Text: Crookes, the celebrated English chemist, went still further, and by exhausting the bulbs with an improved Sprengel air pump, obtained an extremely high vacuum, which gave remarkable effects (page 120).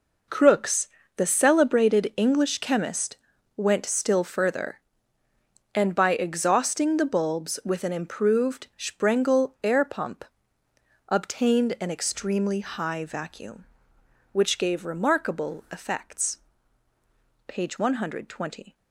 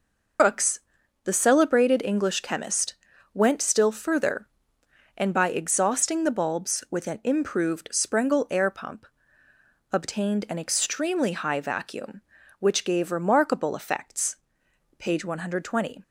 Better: first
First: none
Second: loses the start of "Crookes"; at 0.3 s; 135 ms

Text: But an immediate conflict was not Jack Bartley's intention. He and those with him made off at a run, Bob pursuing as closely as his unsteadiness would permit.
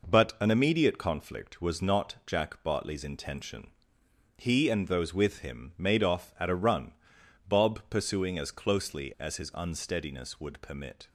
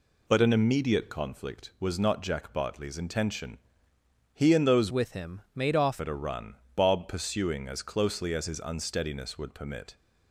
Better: first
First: none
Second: changes voice from "with" to "off"; from 4.9 to 6.0 s; 1.1 s long

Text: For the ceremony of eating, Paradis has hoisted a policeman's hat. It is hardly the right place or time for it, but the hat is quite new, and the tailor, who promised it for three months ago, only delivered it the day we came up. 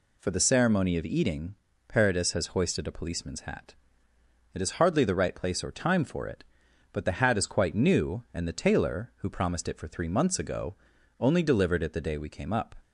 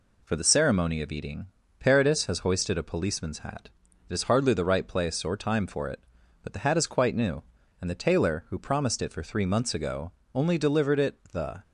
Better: first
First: none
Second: stops before "day we came up"; at 11.6 s

